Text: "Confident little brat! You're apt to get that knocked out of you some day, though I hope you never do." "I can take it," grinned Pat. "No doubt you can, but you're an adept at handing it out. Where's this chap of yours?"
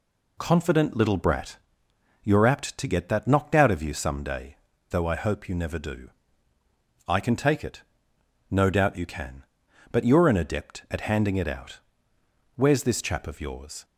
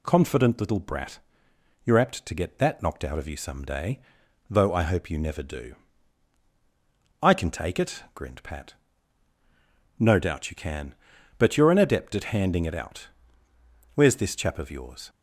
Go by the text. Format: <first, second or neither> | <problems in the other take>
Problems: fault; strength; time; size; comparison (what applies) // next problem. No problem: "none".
second | skips "grinned Pat"; at 8.1 s